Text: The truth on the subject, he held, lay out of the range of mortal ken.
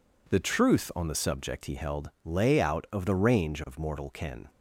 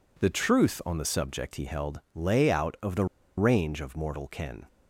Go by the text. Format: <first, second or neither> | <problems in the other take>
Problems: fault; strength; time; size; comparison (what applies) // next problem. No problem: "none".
first | pauses between "the" and "range"; slight; at 3.0 s; 0.32 s long